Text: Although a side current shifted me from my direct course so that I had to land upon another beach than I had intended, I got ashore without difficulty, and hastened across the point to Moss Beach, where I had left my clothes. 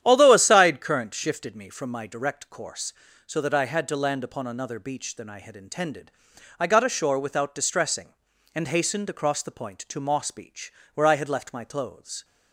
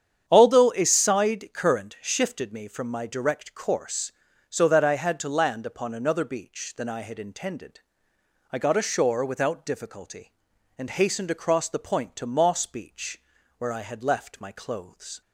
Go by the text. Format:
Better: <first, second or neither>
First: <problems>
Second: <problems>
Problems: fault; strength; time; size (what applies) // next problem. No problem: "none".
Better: second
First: starts louder than the rest; strong; until 1.0 s; 10 dB // says "distressing" for "difficulty"; at 7.5 s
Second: starts louder than the rest; strong; until 1.2 s; 8.5 dB